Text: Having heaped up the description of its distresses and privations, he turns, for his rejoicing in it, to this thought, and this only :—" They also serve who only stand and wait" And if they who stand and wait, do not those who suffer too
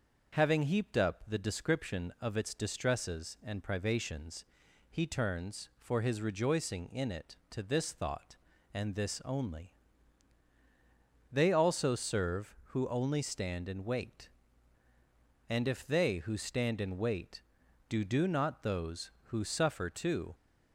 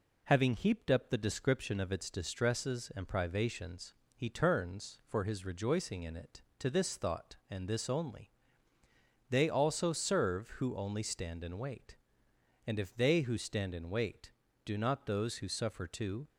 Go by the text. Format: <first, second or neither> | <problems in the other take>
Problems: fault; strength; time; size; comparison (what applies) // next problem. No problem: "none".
second | starts louder than the rest; until 1.4 s; 6 dB // says "do" twice; at 18.0 s